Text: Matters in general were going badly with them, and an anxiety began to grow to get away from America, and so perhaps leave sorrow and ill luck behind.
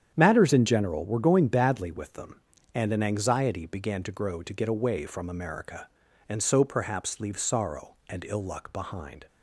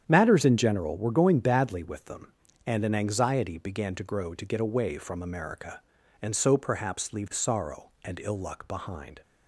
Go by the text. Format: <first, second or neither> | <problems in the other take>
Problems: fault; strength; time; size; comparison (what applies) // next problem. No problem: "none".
neither | starts louder than the rest; strong; the same in both